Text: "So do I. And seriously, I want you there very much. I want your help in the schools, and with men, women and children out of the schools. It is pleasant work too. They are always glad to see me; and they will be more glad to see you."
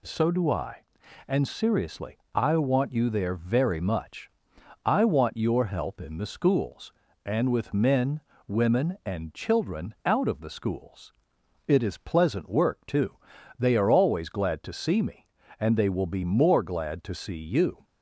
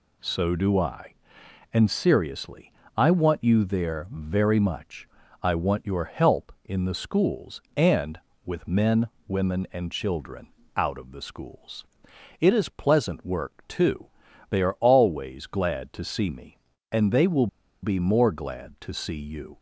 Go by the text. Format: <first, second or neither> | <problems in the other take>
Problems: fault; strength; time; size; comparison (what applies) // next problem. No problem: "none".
first | pauses between "children" and "out"; slight; at 10.4 s; 0.26 s long // pauses between "will" and "be"; slight; at 17.4 s; 0.35 s long